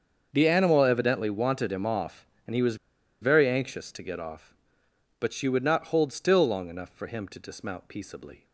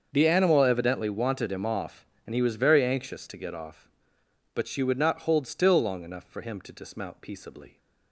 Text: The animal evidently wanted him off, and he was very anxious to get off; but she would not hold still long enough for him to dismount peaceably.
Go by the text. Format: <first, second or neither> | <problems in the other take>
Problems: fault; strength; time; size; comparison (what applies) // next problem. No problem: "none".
second | starts louder than the rest; until 1.3 s; 6.5 dB; also in the second // pauses between "was" and "very"; at 2.7 s; 0.45 s long